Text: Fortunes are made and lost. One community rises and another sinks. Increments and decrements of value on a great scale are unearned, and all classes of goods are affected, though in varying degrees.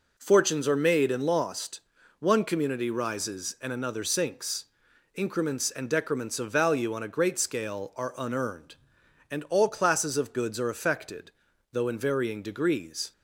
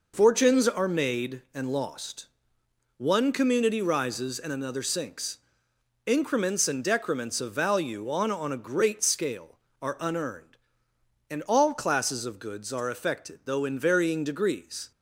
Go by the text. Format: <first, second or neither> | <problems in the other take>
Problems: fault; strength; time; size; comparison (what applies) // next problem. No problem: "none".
first | says "on" twice; at 8.3 s